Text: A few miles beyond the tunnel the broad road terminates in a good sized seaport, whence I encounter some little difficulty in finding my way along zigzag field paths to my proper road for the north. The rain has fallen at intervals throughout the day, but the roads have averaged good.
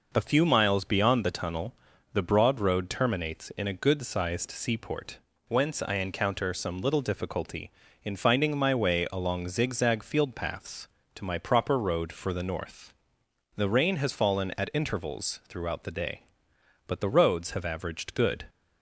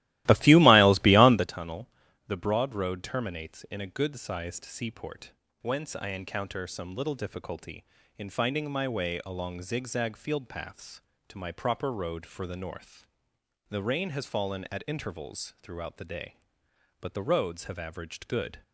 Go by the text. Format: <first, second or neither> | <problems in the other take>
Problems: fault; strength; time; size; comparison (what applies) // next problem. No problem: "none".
first | starts louder than the rest; strong; until 1.5 s; 16.5 dB // pauses between "tunnel" and "the"; at 1.8 s; 0.38 s long; also in the first